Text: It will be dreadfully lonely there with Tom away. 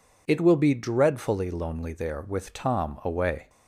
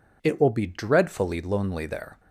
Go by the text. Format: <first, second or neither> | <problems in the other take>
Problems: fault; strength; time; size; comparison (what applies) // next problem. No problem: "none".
first | stops before "with Tom away"; at 2.1 s